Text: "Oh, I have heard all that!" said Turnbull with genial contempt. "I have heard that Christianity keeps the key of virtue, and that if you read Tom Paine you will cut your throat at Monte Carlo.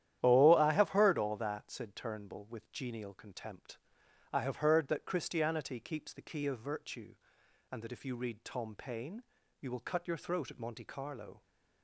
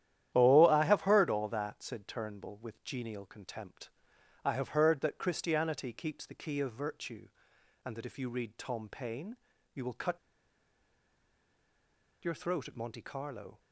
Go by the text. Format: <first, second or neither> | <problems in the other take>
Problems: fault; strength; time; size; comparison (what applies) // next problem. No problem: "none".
first | starts louder than the rest; strong; until 1.3 s; 11.5 dB; strong in the first // pauses between "Paine" and "you"; slight; at 9.3 s; 0.36 s long; slight in the first // pauses between "cut" and "your"; strong; at 10.1 s; 2.0 s long